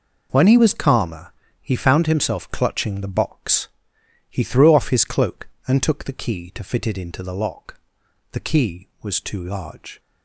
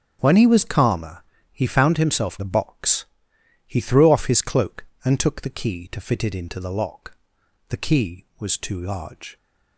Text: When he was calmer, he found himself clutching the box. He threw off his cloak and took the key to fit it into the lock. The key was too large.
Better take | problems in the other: first | starts louder than the rest; strong; until 1.2 s; 7 dB // skips "clutching"; at 2.3 s

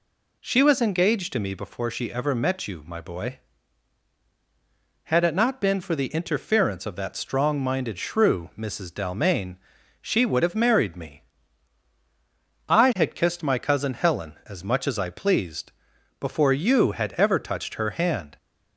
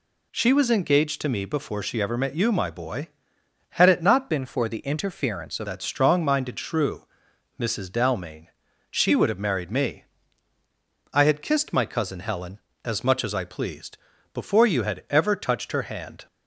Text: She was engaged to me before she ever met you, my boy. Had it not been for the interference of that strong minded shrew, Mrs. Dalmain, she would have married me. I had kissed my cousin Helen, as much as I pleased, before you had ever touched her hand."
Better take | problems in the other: first | changes voice from "been" to "of"; from 4.2 to 5.6 s; 1.4 s long

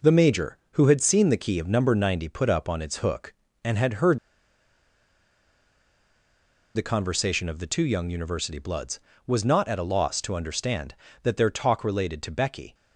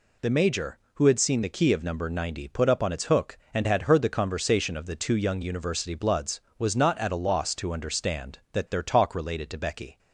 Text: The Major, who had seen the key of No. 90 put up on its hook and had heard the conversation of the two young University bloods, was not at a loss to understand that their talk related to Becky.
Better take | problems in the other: second | pauses between "heard" and "the"; strong; at 4.1 s; 2.5 s long

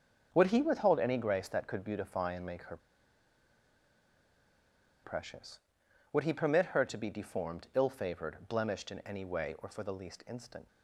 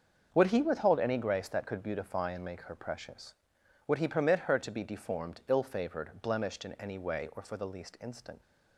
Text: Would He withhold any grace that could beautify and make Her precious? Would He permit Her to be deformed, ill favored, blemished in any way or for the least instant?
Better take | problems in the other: second | starts louder than the rest; until 1.3 s; 6.5 dB; also in the second // pauses between "Her" and "precious"; strong; at 2.7 s; 2.2 s long

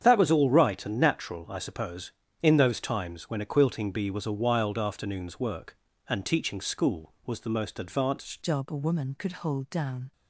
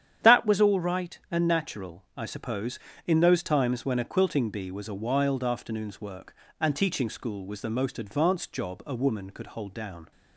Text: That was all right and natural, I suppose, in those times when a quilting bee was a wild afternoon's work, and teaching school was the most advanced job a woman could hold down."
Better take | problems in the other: second | starts louder than the rest; strong; until 1.0 s; 8 dB; strong in the second // changes voice at "job"; from 8.4 s on; 1.7 s long

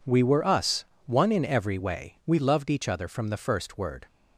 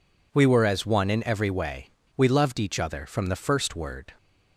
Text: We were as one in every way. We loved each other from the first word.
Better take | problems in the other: second | says "us" for "as"; at 0.4 s

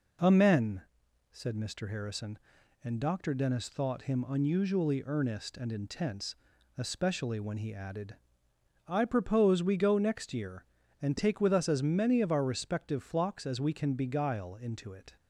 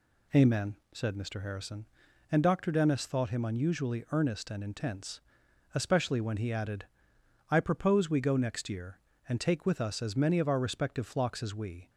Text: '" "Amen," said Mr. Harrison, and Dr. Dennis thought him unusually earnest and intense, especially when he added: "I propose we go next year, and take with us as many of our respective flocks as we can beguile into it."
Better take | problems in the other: first | stops before "can beguile into it"; at 11.8 s

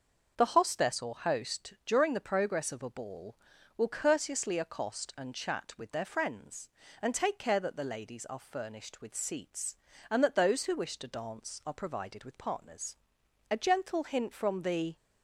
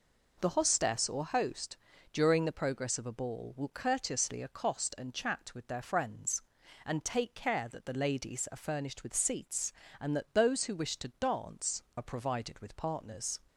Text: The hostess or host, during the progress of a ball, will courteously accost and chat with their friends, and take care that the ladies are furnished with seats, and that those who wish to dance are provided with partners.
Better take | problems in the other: second | starts louder than the rest; until 1.3 s; 6.5 dB // goes on to say "A gentle hint from the"; from 13.5 s on; 1.4 s long

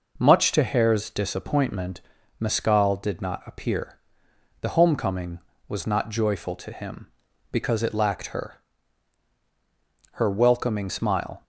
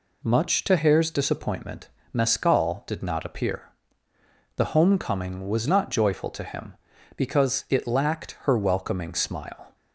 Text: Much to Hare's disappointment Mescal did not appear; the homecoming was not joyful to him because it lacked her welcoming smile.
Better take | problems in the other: second | pauses between "disappointment" and "Mescal"; at 2.0 s; 0.40 s long; slight in the second // says "her" twice; at 10.1 s

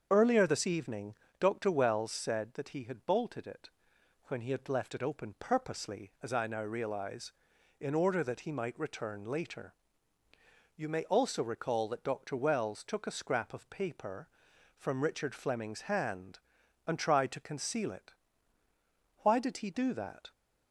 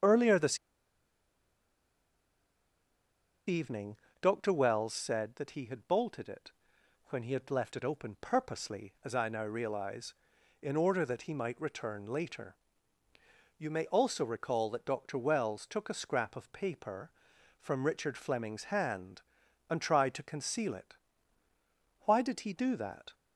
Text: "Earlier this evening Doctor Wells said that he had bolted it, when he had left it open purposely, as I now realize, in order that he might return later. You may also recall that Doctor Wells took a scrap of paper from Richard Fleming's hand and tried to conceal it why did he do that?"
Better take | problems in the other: first | starts louder than the rest; until 3.9 s; 7 dB; also in the first // pauses between "this" and "evening"; strong; at 0.5 s; 2.8 s long // pauses between "evening" and "Doctor"; slight; at 3.9 s; 0.26 s long; slight in the first // pauses between "it" and "why"; at 20.9 s; 1.0 s long; also in the first

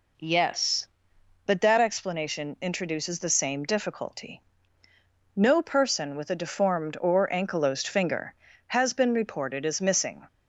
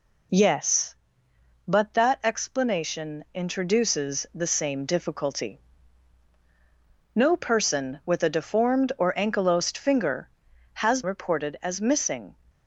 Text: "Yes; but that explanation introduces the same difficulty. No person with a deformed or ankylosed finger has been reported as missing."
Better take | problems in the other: first | skips "been"; at 11.0 s

